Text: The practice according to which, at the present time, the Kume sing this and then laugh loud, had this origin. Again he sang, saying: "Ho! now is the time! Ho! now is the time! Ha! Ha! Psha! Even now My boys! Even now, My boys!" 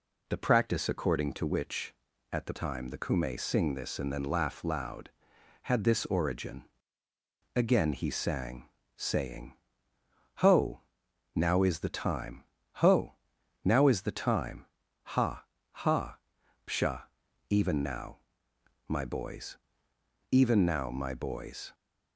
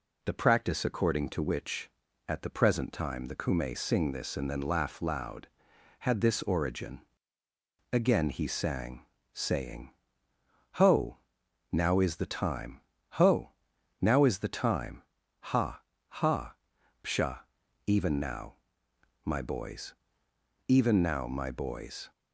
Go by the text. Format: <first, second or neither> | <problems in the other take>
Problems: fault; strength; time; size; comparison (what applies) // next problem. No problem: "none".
second | skips "present"; at 2.5 s // pauses between "now" and "My"; noticeable; at 18.1 s; 0.68 s long; noticeable in the second